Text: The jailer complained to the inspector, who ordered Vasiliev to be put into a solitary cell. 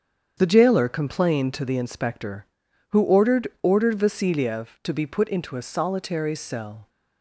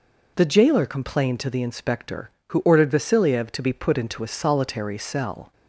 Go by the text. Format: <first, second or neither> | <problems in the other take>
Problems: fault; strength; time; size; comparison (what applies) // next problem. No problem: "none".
second | starts louder than the rest; strong; until 1.3 s; 7.5 dB // says "ordered" twice; at 3.6 s